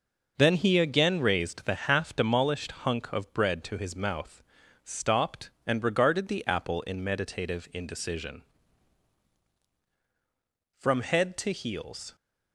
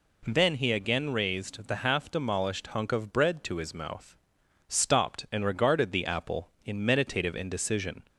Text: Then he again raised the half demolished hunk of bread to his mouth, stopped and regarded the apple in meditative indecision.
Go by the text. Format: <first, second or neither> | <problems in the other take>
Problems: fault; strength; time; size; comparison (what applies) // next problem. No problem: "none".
second | goes on to say "From head to heels"; from 10.7 s on; 1.3 s long